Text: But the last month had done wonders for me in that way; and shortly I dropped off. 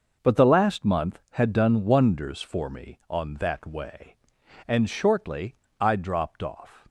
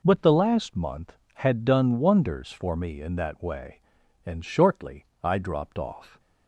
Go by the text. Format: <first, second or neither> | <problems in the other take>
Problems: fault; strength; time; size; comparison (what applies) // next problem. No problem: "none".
second | says "on" for "in"; at 3.0 s // pauses between "shortly" and "I"; slight; at 5.5 s; 0.24 s long; slight in the second